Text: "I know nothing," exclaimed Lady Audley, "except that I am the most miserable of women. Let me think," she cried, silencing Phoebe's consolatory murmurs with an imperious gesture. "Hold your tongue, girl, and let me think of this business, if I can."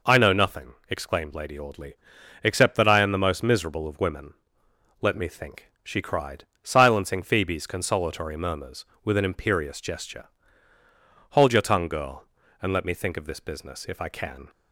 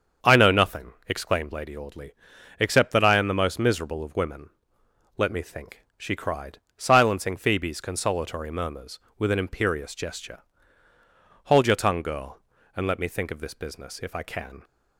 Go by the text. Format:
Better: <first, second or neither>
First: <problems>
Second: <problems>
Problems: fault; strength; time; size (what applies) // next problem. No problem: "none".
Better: first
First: none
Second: starts louder than the rest; until 1.7 s; 7 dB